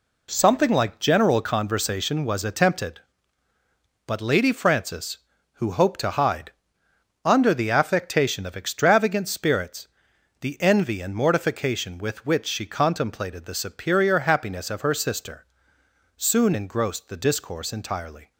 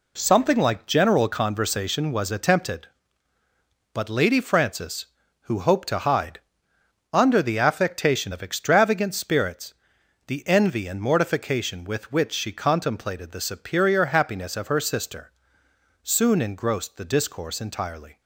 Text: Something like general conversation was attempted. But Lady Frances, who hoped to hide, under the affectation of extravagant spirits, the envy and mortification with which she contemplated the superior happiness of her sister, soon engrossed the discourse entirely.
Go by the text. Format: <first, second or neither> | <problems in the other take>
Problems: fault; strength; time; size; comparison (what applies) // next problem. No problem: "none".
neither | none